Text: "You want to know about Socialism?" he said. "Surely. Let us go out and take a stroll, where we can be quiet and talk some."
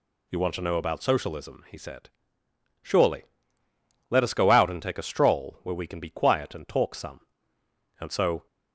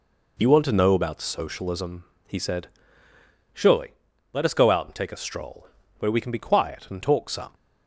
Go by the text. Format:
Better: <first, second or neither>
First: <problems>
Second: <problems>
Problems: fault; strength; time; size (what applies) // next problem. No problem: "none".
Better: second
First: goes on to say "And so"; slight; from 8.0 s on; 0.46 s long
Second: none